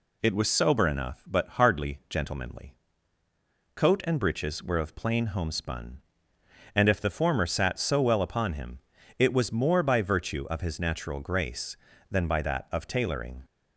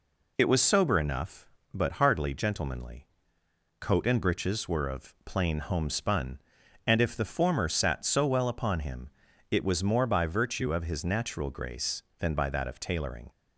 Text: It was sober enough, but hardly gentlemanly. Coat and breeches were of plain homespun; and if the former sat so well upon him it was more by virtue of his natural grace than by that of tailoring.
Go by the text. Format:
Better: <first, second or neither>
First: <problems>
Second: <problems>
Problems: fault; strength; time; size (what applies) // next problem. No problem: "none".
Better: neither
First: pauses between "him" and "it"; at 8.7 s; 0.38 s long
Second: pauses between "him" and "it"; at 9.0 s; 0.42 s long